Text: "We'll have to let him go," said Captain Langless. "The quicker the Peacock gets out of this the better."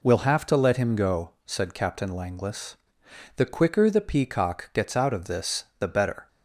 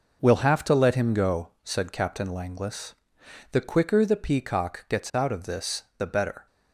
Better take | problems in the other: first | gets quieter; strong; throughout; 9 dB // pauses between "this" and "the"; slight; at 5.8 s; 0.16 s long; slight in the first

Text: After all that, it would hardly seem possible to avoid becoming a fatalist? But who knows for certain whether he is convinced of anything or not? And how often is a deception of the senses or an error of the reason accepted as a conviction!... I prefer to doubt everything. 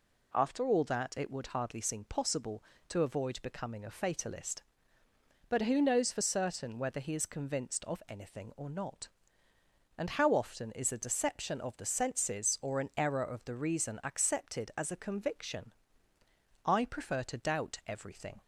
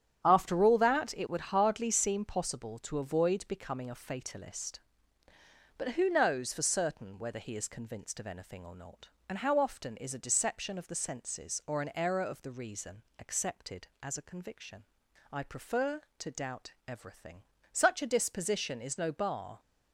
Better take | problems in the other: first | starts louder than the rest; strong; until 1.2 s; 9.5 dB // pauses between "reason" and "accepted"; slight; at 13.0 s; 0.18 s long // pauses between "doubt" and "everything"; slight; at 16.7 s; 0.16 s long // goes on to say "Such a disposition is no bar"; strong; from 17.7 s on; 1.8 s long

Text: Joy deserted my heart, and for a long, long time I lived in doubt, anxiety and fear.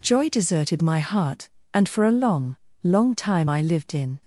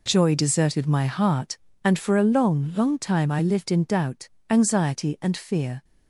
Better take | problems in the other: second | stops before "doubt anxiety and fear"; at 4.2 s

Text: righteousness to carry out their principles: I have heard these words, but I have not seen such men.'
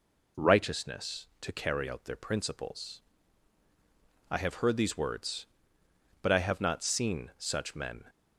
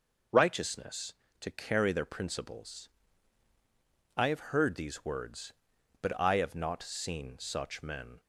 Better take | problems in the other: first | skips "out"; at 1.9 s

